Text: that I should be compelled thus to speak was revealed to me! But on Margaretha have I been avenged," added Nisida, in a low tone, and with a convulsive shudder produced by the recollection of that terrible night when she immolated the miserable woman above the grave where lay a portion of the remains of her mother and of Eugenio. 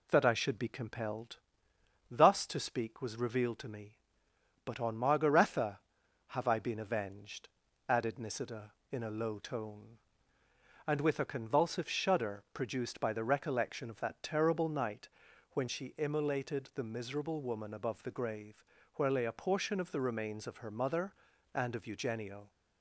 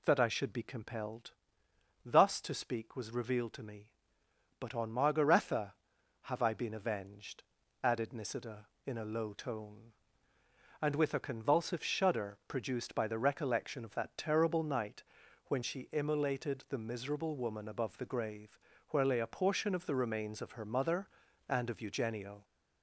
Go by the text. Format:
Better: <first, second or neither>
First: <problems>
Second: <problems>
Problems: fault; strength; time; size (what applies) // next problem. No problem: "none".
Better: first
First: pauses between "compelled" and "thus"; noticeable; at 1.3 s; 0.72 s long // pauses between "night" and "when"; noticeable; at 15.0 s; 0.46 s long // pauses between "grave" and "where"; slight; at 18.6 s; 0.30 s long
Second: gets louder; slight; throughout; 2.5 dB // pauses between "compelled" and "thus"; noticeable; at 1.3 s; 0.72 s long // pauses between "night" and "when"; noticeable; at 15.0 s; 0.46 s long // pauses between "grave" and "where"; slight; at 18.5 s; 0.30 s long